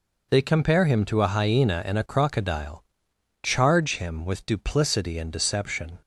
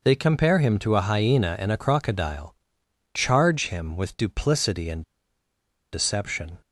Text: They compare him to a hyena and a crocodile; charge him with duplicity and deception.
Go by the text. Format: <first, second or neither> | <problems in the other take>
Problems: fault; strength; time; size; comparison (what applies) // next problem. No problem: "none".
first | pauses between "and" and "deception"; noticeable; at 5.0 s; 0.91 s long